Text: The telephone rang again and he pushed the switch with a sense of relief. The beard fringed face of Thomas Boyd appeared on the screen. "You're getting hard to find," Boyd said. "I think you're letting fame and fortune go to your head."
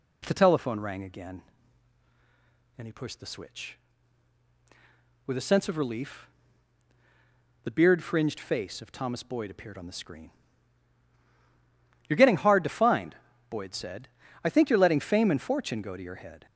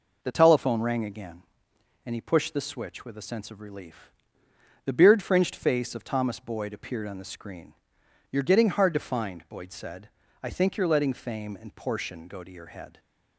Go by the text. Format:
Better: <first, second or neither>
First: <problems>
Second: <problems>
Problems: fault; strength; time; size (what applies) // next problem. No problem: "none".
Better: first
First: none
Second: says "portion" for "fortune"; at 11.7 s